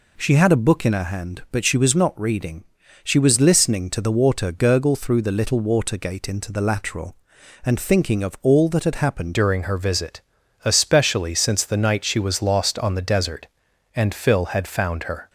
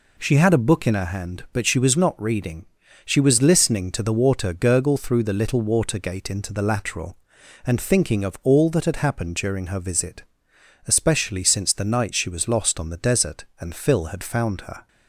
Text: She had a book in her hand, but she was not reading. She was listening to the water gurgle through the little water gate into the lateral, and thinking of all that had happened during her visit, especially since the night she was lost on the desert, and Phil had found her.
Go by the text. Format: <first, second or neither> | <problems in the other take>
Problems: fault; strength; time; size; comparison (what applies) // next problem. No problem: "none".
second | changes voice at "during"; from 9.3 s on; 5.9 s long